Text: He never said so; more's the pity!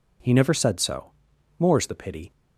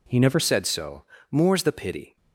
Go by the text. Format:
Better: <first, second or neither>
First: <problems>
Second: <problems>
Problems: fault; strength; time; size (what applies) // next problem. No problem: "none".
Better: first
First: none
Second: changes voice at "said"; from 0.3 s on; 1.8 s long